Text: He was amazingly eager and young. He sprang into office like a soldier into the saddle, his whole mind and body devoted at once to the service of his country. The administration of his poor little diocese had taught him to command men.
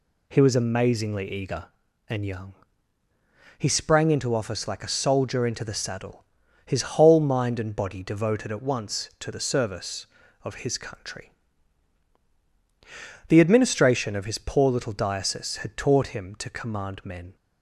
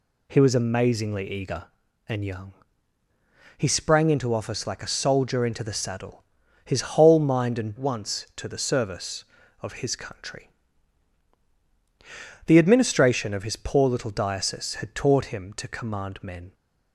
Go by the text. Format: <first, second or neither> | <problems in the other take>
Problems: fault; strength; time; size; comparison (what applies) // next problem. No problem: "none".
first | skips "body devoted at"; at 7.7 s